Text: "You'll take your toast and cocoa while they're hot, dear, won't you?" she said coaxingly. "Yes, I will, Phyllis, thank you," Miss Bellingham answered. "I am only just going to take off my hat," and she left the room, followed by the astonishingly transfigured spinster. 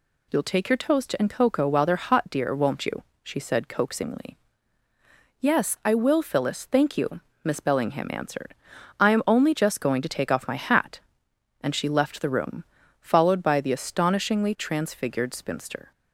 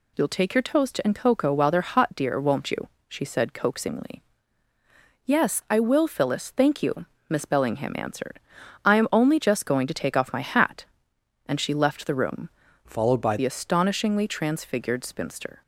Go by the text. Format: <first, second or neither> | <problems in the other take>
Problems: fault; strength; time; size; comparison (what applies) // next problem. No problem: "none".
first | changes voice from "followed" to "by"; from 12.8 to 13.3 s; 0.5 s long